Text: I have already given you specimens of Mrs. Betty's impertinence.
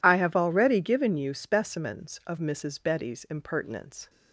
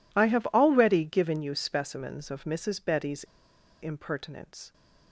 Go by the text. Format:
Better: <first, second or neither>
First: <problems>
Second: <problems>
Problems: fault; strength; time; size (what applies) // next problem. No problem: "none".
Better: first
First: none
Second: pauses between "Betty's" and "impertinence"; noticeable; at 3.2 s; 0.58 s long